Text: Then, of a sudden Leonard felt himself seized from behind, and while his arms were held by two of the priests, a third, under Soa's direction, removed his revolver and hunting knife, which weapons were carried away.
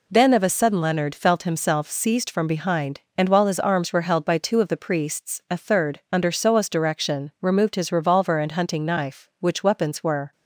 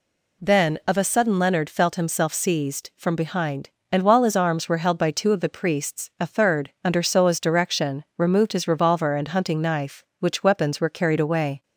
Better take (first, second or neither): second